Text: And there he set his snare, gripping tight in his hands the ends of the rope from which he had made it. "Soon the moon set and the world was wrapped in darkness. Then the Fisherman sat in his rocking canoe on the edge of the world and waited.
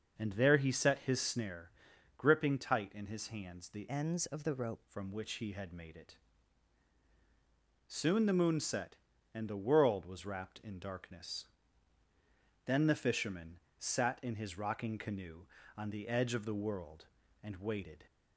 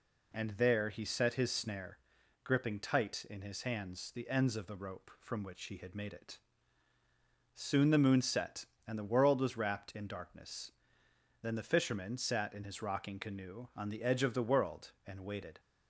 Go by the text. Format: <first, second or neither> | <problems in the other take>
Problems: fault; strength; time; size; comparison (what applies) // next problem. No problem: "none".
second | starts louder than the rest; noticeable; until 1.1 s; 6 dB // changes voice from "ends" to "rope"; from 3.8 to 4.8 s; 1.0 s long // pauses between "Fisherman" and "sat"; slight; at 13.5 s; 0.20 s long